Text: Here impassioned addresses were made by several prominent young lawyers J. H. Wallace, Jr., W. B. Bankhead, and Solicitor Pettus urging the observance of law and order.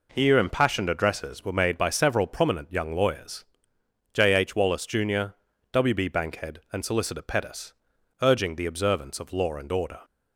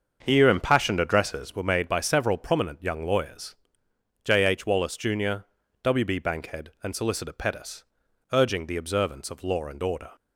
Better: first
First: pauses between "lawyers" and "J"; noticeable; at 3.4 s; 0.68 s long // pauses between "Pettus" and "urging"; noticeable; at 7.7 s; 0.48 s long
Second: starts louder than the rest; until 1.7 s; 6.5 dB // pauses between "lawyers" and "J"; noticeable; at 3.5 s; 0.68 s long // pauses between "Pettus" and "urging"; noticeable; at 7.8 s; 0.48 s long

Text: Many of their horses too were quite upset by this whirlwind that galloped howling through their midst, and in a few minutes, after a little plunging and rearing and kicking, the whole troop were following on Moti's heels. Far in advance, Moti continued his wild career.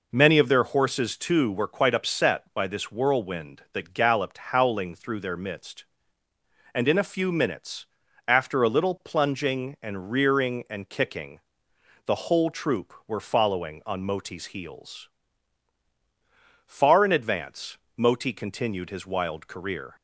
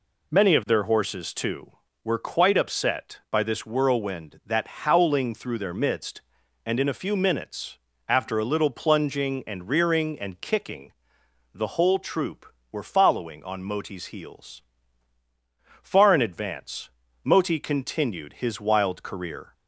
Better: first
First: none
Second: skips "galloped"; at 4.6 s

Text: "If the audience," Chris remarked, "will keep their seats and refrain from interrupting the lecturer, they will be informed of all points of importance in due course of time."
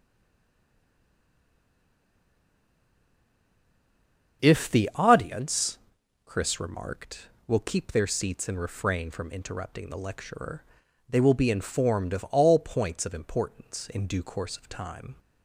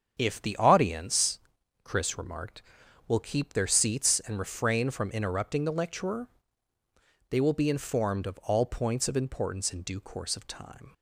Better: second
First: stays silent before the first word; strong; until 4.4 s; 4.4 s long // starts louder than the rest; until 5.4 s; 7 dB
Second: starts louder than the rest; strong; until 1.1 s; 7.5 dB

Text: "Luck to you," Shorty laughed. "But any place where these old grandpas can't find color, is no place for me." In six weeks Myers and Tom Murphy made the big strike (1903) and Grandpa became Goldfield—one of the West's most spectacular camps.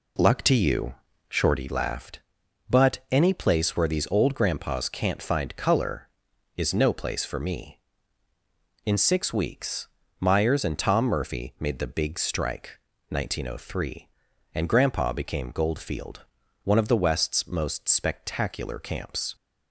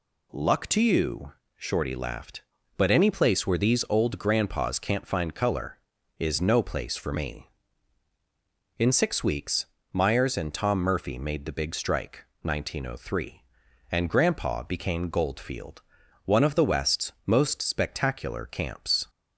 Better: second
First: starts louder than the rest; slight; until 1.7 s; 3 dB // pauses between "weeks" and "Myers"; slight; at 9.8 s; 0.32 s long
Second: pauses between "weeks" and "Myers"; slight; at 9.6 s; 0.26 s long

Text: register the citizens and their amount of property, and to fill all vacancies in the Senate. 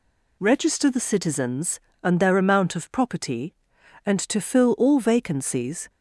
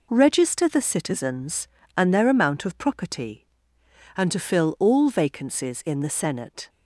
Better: second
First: stops before "in the Senate"; at 5.8 s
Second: none

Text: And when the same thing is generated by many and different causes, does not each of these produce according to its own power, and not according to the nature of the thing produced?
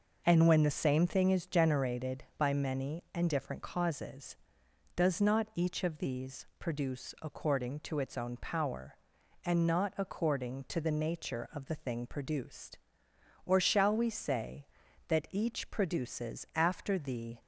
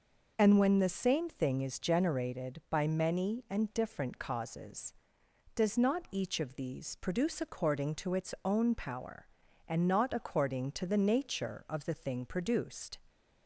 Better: second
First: goes on to say "Or shall we say that each produces after the"; strong; from 13.4 s on; 3.9 s long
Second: none

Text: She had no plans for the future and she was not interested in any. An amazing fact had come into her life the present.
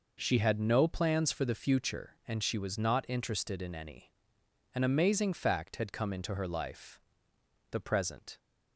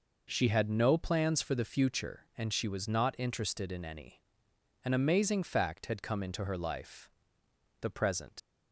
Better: first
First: pauses between "life" and "the"; noticeable; at 6.9 s; 0.72 s long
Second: pauses between "life" and "the"; noticeable; at 7.0 s; 0.72 s long // leaves "present" unfinished; at 8.3 s; 85 ms

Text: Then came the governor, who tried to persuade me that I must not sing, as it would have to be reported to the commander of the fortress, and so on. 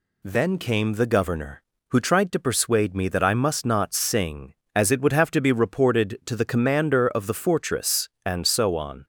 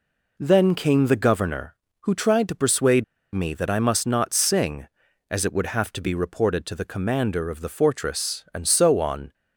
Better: first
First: none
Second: pauses between "persuade" and "me"; slight; at 3.0 s; 0.30 s long

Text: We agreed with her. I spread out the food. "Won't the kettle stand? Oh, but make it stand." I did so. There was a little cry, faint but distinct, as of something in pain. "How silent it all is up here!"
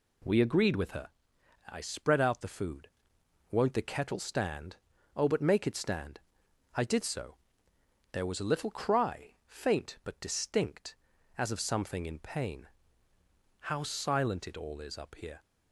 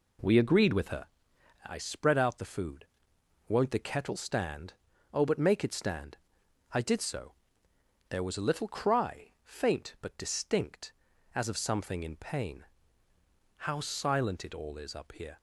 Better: first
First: none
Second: starts louder than the rest; slight; until 2.0 s; 3 dB

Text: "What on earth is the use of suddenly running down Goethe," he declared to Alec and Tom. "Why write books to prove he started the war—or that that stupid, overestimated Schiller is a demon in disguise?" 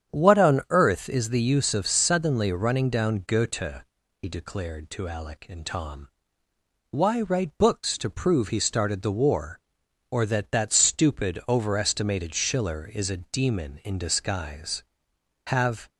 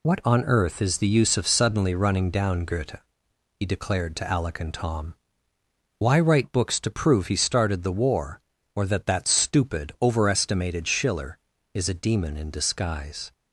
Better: second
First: starts louder than the rest; strong; until 1.2 s; 8.5 dB // goes on to say "Have"; slight; from 15.4 s on; 0.42 s long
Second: none

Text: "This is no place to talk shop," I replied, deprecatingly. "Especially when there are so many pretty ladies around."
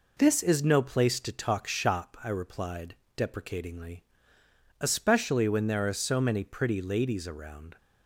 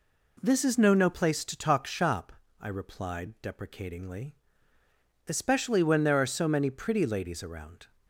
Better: first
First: none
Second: says "no" twice; at 0.9 s

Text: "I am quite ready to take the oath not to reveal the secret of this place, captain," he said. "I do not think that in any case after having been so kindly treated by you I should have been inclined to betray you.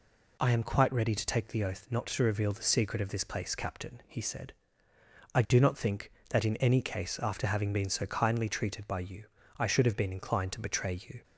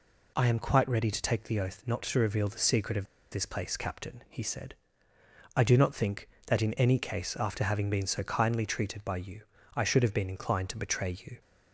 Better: first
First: pauses between "you" and "I"; slight; at 9.2 s; 0.32 s long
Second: pauses between "of" and "this"; slight; at 3.0 s; 0.26 s long // pauses between "you" and "I"; slight; at 9.4 s; 0.32 s long

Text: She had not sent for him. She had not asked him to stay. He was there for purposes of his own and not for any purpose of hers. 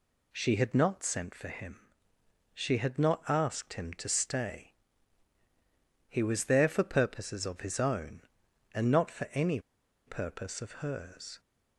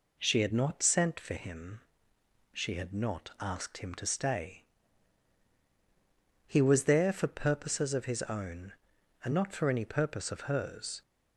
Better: second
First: pauses between "any" and "purpose"; noticeable; at 9.5 s; 0.47 s long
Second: none

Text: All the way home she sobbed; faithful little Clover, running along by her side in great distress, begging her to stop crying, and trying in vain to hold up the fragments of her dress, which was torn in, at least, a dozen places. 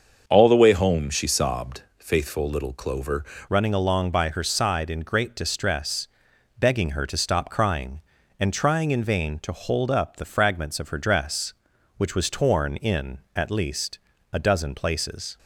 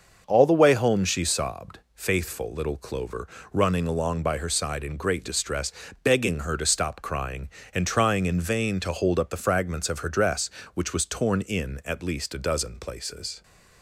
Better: second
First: starts louder than the rest; until 1.2 s; 6.5 dB // changes voice at "running"; from 3.4 s on; 11.9 s long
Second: starts louder than the rest; until 1.2 s; 6 dB

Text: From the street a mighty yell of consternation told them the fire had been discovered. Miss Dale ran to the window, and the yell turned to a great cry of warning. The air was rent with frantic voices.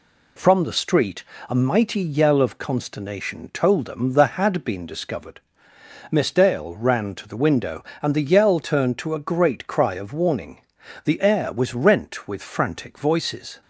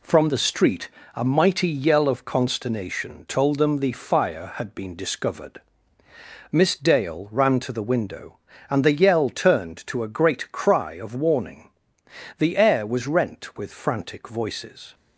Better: second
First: pauses between "street" and "a"; slight; at 1.2 s; 0.26 s long // skips "fire"; at 4.3 s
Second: pauses between "street" and "a"; slight; at 0.8 s; 0.26 s long

